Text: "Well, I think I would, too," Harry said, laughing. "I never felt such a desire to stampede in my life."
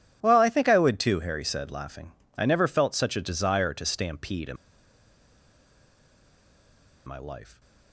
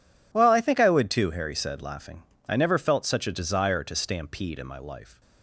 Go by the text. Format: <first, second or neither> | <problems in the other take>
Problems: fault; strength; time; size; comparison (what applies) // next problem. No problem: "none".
second | pauses between "in" and "my"; strong; at 4.5 s; 2.4 s long